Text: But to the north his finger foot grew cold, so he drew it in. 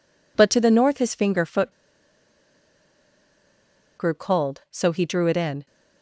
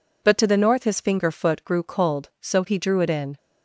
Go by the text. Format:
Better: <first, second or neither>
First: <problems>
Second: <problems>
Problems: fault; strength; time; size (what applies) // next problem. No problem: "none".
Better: second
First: pauses between "foot" and "grew"; strong; at 1.7 s; 2.2 s long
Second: none